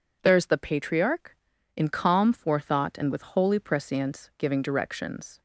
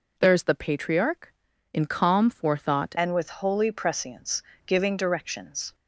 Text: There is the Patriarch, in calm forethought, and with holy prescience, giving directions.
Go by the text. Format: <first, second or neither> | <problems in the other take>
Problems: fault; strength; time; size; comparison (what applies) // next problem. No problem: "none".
first | changes voice at "and"; from 2.9 s on; 2.8 s long